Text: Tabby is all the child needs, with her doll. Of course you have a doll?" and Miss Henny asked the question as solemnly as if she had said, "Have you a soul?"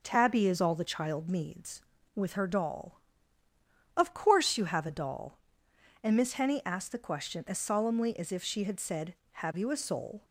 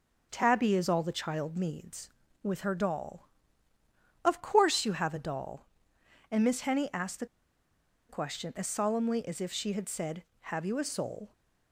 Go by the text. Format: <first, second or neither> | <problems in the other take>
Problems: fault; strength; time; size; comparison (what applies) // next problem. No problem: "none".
first | pauses between "the" and "question"; noticeable; at 7.2 s; 0.83 s long